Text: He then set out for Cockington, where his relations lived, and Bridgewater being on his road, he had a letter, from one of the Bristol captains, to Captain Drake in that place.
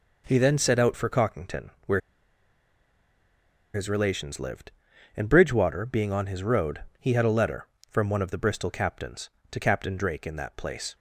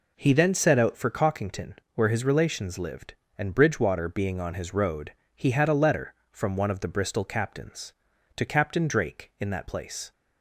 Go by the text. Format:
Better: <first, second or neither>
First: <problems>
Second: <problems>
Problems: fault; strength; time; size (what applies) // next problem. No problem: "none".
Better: second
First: pauses between "where" and "his"; strong; at 2.0 s; 1.7 s long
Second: none